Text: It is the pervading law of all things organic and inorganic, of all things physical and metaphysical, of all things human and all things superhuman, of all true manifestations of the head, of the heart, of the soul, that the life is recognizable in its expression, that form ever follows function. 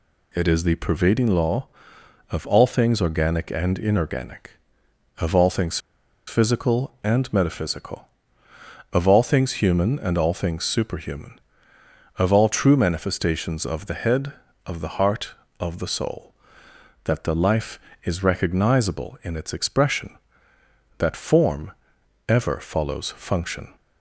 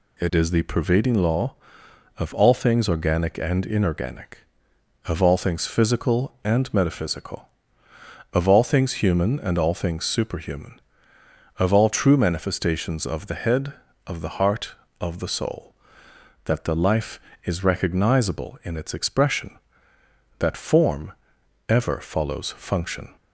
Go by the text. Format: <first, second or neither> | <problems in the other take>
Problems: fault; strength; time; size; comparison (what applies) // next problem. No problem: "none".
second | pauses between "things" and "physical"; noticeable; at 5.7 s; 0.48 s long // pauses between "form" and "ever"; noticeable; at 21.7 s; 0.56 s long; noticeable in the second